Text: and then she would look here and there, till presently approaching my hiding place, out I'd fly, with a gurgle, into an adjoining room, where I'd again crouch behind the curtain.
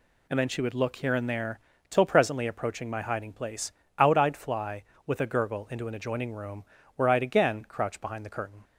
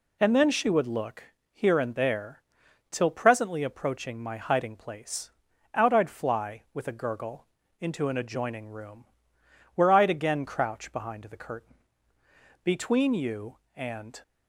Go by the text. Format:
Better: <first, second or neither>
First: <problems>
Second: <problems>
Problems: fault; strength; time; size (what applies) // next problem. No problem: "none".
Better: first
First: none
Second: pauses between "look" and "here"; slight; at 1.2 s; 0.28 s long // goes on to say "Between you and"; from 12.6 s on; 1.5 s long